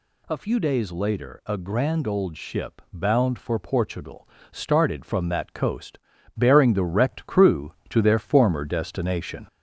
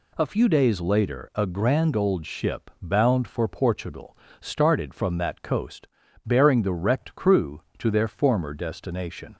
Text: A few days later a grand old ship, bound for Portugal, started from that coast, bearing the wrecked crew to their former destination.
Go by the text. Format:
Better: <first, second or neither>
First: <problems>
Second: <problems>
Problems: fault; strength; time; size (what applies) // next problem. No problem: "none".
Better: second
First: gets louder; slight; throughout; 2 dB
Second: none